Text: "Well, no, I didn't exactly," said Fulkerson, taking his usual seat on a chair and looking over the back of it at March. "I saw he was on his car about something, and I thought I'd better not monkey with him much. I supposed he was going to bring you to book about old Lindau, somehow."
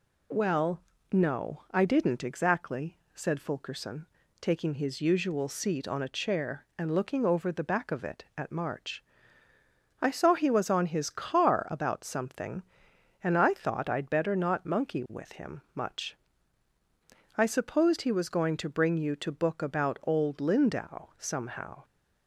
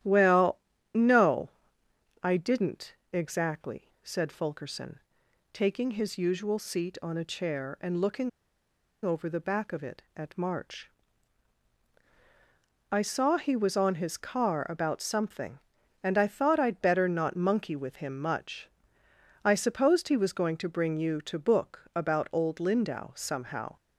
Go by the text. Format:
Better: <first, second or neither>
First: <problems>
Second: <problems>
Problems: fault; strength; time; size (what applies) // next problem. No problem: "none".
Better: first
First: none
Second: starts louder than the rest; strong; until 1.3 s; 11.5 dB // pauses between "didn't" and "exactly"; slight; at 2.9 s; 0.18 s long // pauses between "looking" and "over"; noticeable; at 8.2 s; 0.76 s long